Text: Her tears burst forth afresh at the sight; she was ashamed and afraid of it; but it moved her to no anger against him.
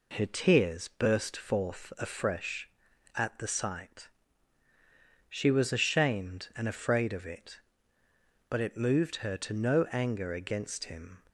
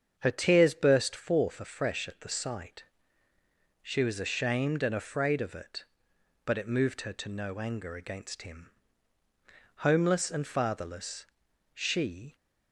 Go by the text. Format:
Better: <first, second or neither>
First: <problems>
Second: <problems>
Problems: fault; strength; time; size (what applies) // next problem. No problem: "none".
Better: first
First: none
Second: starts louder than the rest; strong; until 1.2 s; 7 dB // goes on to say "Homeless and fatherless she"; strong; from 9.7 s on; 2.6 s long